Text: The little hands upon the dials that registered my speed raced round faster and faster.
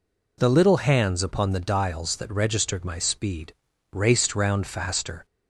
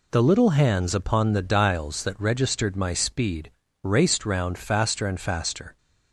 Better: second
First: pauses between "speed" and "raced"; at 3.5 s; 0.38 s long // stops before "and faster"; at 5.2 s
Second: pauses between "speed" and "raced"; slight; at 3.4 s; 0.32 s long

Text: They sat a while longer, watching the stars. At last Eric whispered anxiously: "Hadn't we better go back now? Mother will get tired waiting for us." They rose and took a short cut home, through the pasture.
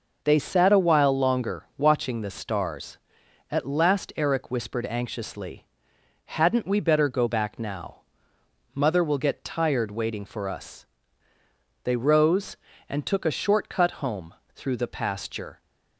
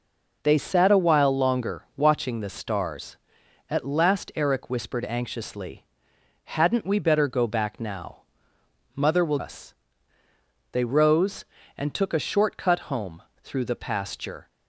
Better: first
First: none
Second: skips "get tired waiting for"; at 9.3 s

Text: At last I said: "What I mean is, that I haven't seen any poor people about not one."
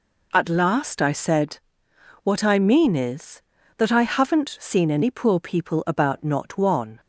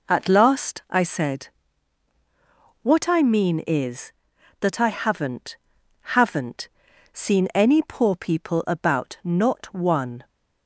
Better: first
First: none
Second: says "haven't" twice; at 6.1 s

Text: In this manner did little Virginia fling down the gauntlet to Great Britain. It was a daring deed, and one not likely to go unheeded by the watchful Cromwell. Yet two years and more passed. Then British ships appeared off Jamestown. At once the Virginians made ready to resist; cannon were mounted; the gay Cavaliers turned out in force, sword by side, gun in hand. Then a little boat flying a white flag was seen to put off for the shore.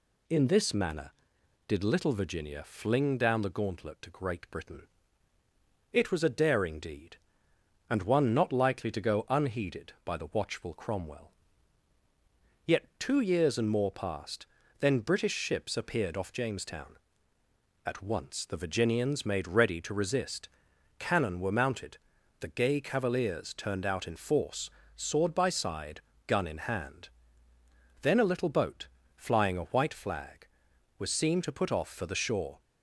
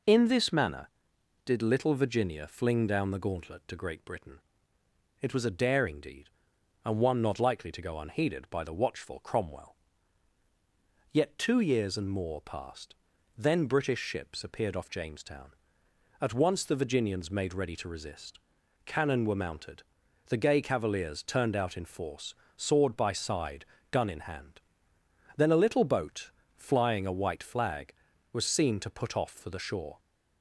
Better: neither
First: pauses between "boat" and "flying"; slight; at 28.8 s; 0.28 s long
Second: pauses between "boat" and "flying"; slight; at 26.3 s; 0.26 s long

